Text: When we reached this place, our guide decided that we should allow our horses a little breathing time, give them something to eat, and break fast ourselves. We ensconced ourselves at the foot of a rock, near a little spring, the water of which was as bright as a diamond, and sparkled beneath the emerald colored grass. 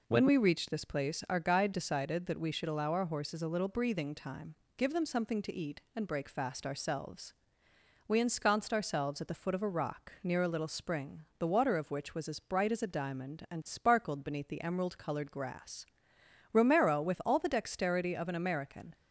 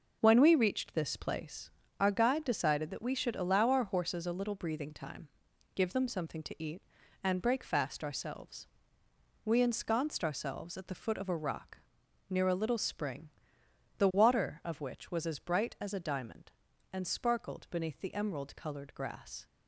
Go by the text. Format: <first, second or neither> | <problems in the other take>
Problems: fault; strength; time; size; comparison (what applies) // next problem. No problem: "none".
second | goes on to say "Romero with all the dexterity of an American"; strong; from 16.5 s on; 2.4 s long